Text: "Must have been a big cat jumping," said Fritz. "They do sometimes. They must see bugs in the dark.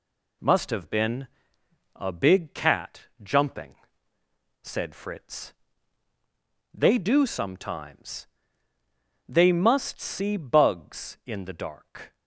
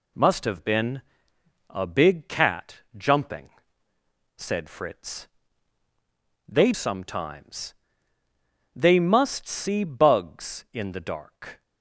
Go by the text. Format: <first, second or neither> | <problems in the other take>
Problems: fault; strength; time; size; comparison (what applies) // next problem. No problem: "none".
first | pauses between "been" and "a"; noticeable; at 1.0 s; 0.70 s long; noticeable in the first // skips "do"; at 6.7 s